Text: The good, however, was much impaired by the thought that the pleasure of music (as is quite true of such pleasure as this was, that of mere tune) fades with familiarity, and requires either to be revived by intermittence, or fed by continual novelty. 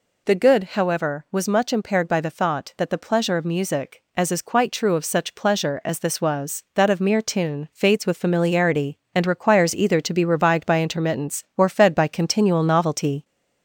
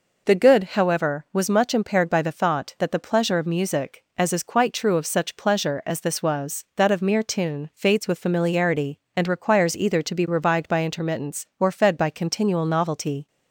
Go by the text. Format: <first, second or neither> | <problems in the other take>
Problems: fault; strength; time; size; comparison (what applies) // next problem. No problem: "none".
second | gets louder; slight; throughout; 2.5 dB